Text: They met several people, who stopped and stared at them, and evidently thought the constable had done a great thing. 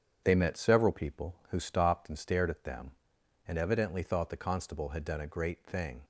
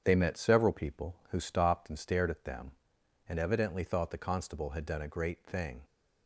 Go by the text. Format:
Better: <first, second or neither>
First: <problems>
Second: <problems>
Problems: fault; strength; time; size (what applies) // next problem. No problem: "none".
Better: neither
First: starts louder than the rest; strong; until 1.2 s; 8 dB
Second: starts louder than the rest; strong; until 1.0 s; 8 dB